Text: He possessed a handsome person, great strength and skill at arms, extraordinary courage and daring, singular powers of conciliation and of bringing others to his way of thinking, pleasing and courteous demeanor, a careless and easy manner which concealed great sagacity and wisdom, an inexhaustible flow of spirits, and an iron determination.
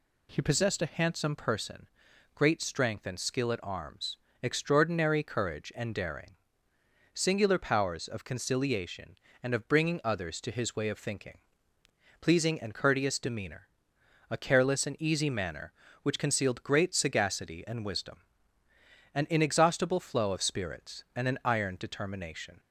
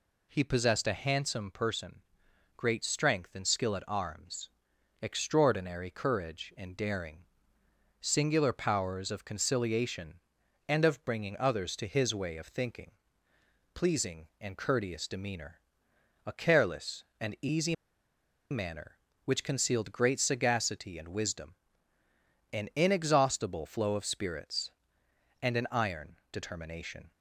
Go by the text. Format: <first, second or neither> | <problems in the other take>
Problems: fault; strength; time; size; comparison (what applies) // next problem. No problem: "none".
first | pauses between "easy" and "manner"; noticeable; at 17.7 s; 0.76 s long // pauses between "iron" and "determination"; slight; at 26.1 s; 0.16 s long